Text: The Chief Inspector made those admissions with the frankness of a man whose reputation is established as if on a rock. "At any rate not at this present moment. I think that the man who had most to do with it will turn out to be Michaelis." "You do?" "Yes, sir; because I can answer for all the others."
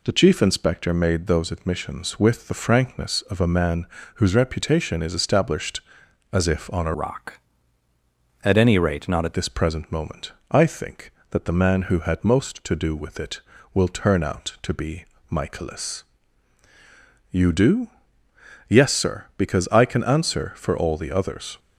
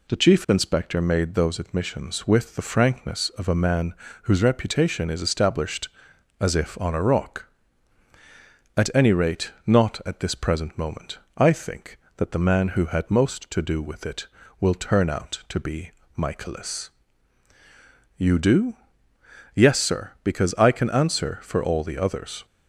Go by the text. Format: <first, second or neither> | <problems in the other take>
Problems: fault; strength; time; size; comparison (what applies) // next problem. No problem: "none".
second | pauses between "man" and "whose"; slight; at 3.8 s; 0.30 s long; slight in the second // changes voice from "rock" to "at"; from 6.9 to 9.3 s; 2.4 s long // pauses between "be" and "Michaelis"; slight; at 15.0 s; 0.24 s long; slight in the second